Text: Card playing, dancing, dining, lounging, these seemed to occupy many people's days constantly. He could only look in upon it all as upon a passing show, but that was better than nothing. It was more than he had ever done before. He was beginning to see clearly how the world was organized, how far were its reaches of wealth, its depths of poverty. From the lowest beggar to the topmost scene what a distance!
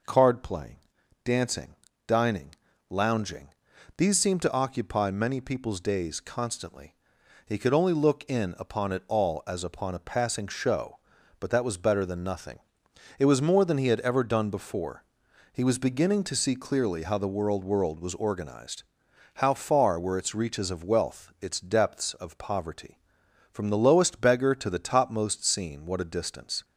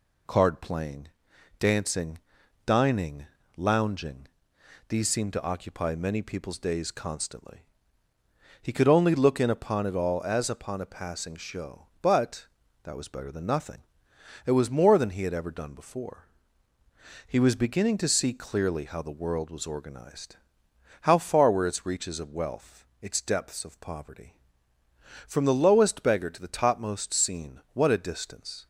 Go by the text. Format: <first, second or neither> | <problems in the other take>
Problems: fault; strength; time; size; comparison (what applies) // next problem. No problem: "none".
second | says "world" twice; at 17.6 s